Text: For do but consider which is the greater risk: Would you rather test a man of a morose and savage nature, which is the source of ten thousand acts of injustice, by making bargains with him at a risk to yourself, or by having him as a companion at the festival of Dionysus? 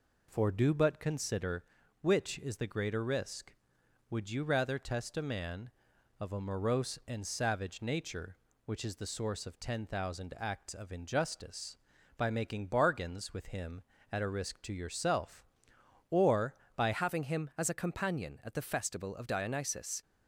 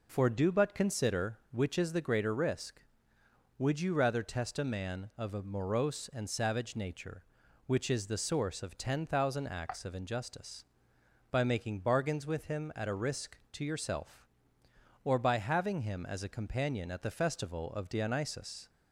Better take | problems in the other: second | changes voice at "having"; from 16.9 s on; 3.1 s long

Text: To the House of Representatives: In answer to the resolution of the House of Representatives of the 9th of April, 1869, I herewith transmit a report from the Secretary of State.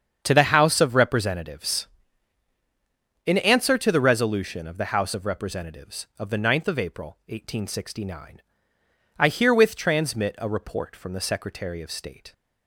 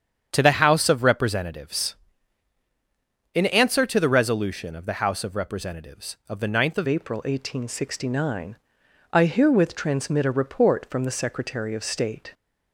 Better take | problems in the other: first | starts louder than the rest; strong; until 1.3 s; 8 dB; strong in the first // changes voice at "April"; from 6.8 s on; 5.5 s long

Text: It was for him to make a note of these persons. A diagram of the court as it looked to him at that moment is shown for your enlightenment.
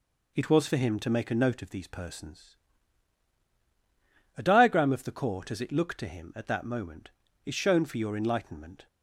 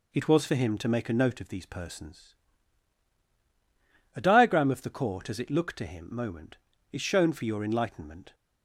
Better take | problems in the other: first | skips "at that"; at 6.1 s

